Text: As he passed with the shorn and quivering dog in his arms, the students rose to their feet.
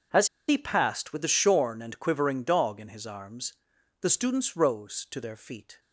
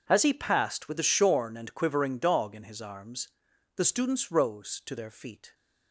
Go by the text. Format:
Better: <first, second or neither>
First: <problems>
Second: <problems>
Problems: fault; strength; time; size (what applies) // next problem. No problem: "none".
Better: second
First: pauses between "As" and "he"; slight; at 0.2 s; 0.22 s long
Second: none